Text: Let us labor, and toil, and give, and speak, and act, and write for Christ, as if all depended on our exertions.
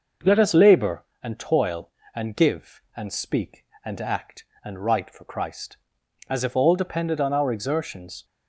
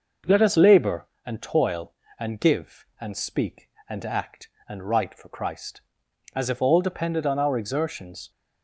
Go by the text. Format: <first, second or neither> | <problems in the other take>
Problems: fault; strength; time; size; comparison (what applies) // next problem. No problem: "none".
neither | none